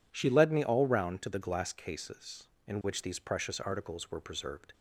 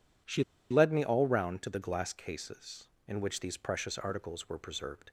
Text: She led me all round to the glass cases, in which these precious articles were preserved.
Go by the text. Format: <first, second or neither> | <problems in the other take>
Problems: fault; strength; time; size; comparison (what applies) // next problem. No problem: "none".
first | pauses between "She" and "led"; slight; at 0.4 s; 0.28 s long